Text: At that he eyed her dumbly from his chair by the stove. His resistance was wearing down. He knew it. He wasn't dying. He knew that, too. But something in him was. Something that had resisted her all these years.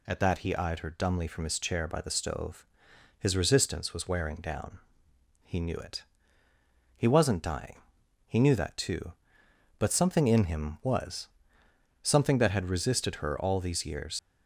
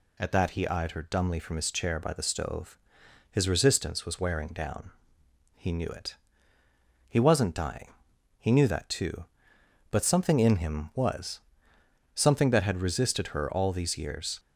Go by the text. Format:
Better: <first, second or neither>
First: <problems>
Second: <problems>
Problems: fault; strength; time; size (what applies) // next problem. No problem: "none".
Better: second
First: leaves "years" unfinished; at 14.1 s; 80 ms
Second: none